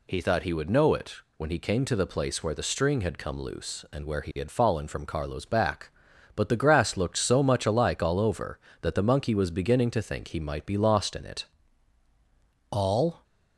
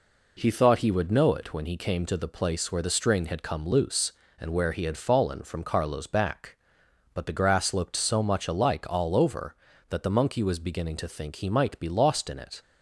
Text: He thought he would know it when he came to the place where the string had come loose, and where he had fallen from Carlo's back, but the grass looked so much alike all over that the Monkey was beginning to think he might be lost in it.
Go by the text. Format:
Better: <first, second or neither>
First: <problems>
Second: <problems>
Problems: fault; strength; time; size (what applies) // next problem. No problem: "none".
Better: second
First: pauses between "it" and "when"; slight; at 1.1 s; 0.20 s long // goes on to say "All"; from 12.6 s on; 0.54 s long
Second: none